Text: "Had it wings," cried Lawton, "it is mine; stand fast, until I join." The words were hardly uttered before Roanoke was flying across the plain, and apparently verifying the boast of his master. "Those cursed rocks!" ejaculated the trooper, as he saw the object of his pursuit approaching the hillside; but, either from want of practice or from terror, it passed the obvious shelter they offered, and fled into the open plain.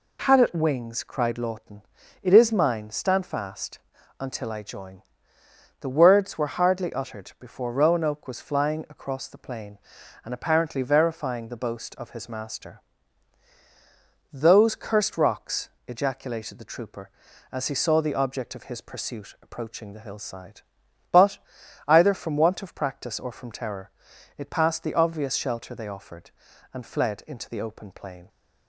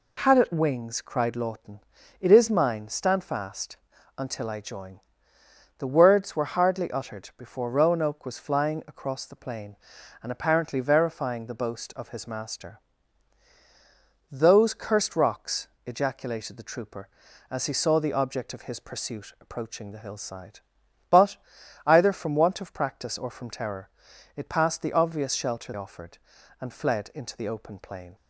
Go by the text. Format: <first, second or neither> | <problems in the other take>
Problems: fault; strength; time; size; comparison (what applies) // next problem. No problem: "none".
first | skips "they"; at 25.7 s